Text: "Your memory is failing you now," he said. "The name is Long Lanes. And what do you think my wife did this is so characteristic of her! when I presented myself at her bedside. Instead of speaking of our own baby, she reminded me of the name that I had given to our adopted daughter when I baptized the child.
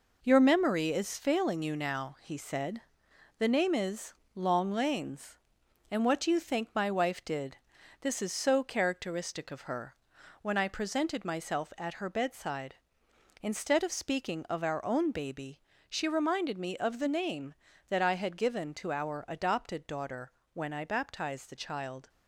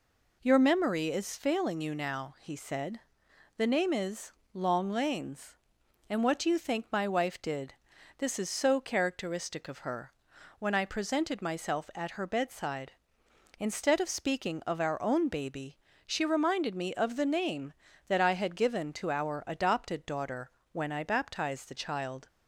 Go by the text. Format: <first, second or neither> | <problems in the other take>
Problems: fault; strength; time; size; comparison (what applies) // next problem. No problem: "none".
second | gets quieter; throughout; 6.5 dB // pauses between "is" and "Long"; slight; at 4.1 s; 0.22 s long; slight in the second // pauses between "did" and "this"; noticeable; at 7.5 s; 0.46 s long; noticeable in the second // pauses between "daughter" and "when"; slight; at 20.3 s; 0.20 s long; slight in the second